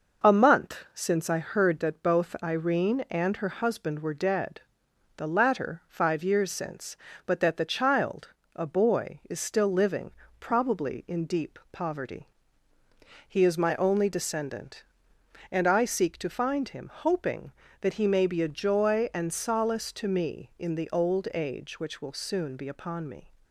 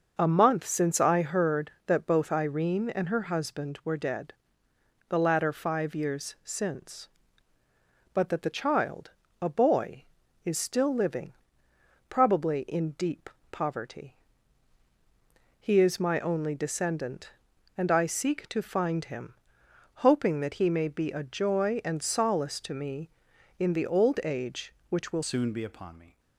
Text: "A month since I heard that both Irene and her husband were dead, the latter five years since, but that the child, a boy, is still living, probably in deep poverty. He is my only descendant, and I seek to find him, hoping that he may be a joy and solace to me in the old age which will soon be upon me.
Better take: first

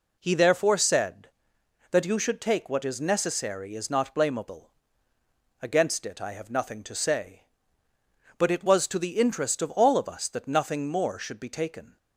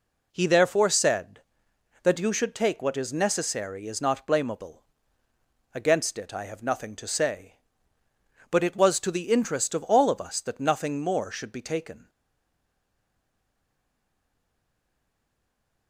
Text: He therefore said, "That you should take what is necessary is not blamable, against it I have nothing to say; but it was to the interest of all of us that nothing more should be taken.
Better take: first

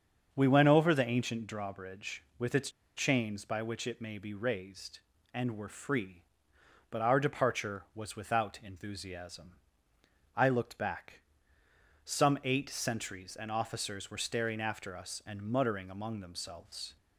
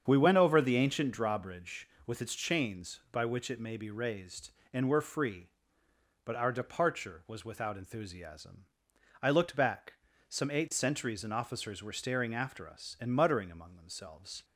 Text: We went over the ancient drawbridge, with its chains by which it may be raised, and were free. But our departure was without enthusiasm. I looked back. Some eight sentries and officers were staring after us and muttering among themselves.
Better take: second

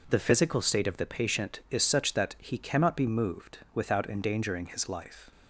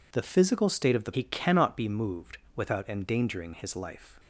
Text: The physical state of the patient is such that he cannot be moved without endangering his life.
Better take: first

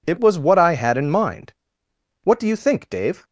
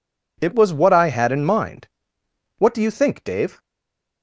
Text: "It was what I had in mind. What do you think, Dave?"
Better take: first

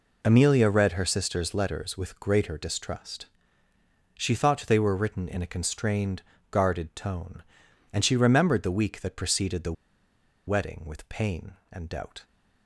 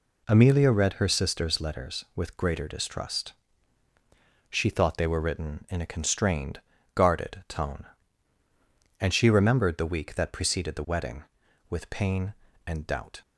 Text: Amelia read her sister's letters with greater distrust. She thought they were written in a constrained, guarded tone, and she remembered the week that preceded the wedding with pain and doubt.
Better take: second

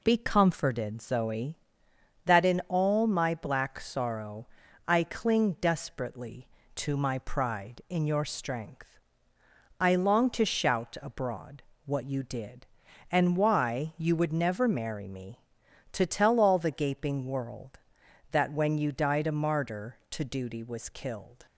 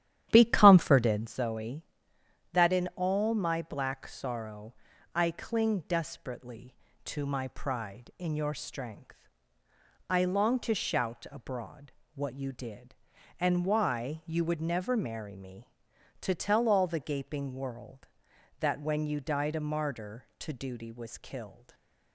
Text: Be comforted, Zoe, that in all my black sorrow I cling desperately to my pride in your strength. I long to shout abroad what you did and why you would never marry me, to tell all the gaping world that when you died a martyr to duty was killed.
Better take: first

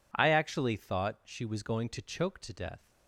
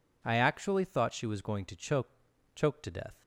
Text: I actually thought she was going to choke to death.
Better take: first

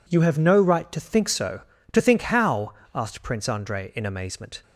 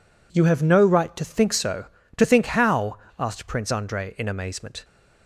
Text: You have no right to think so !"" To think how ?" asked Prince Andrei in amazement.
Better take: neither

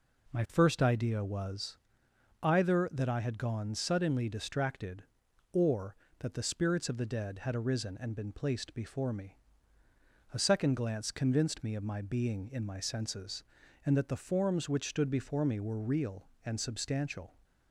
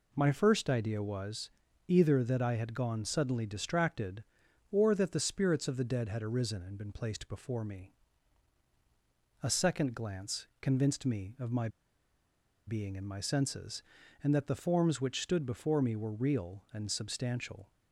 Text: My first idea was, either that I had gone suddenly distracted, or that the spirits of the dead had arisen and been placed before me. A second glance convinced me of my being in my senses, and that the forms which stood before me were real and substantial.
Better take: first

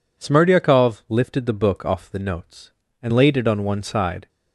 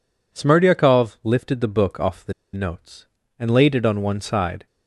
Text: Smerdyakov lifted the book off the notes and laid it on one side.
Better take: first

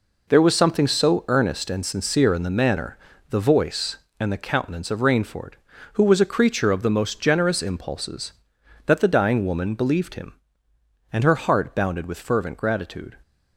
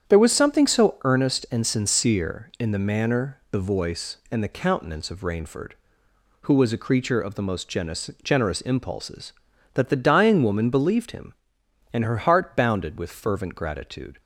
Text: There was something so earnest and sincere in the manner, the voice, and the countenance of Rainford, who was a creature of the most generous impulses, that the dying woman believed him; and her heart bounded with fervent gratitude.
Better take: first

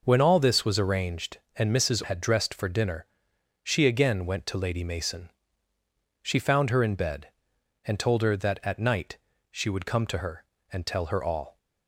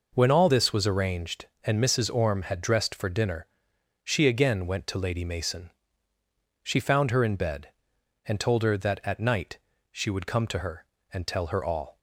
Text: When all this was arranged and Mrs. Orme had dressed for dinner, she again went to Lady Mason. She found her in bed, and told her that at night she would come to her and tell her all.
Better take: second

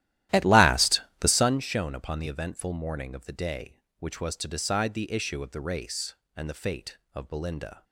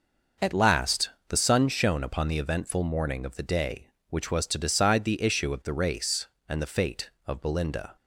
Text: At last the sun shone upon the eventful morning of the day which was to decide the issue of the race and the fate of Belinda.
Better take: second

